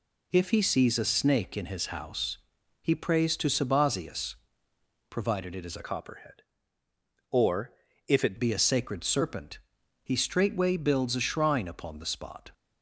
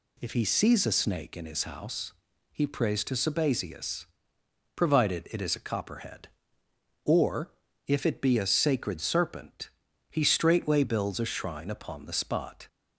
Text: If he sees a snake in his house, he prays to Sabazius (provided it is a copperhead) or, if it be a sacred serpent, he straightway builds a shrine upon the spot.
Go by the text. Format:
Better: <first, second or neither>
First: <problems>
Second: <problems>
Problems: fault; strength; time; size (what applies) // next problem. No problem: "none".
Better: second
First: changes voice from "copperhead" to "it"; from 5.8 to 8.3 s; 2.5 s long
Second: none